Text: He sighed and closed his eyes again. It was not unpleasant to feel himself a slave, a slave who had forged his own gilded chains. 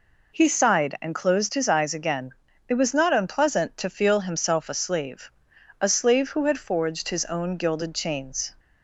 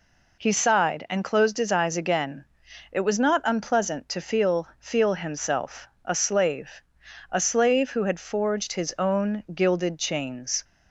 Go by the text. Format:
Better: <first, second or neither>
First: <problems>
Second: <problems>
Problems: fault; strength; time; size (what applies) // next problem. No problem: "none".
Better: first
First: none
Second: says "feel" twice; at 4.7 s // pauses between "himself" and "a"; slight; at 5.8 s; 0.16 s long